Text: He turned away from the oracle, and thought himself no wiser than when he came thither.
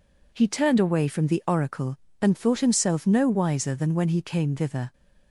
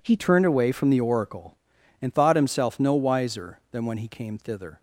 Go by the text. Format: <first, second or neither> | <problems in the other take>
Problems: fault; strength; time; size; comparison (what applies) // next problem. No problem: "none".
first | changes voice at "turned"; from 0.1 s on; 4.7 s long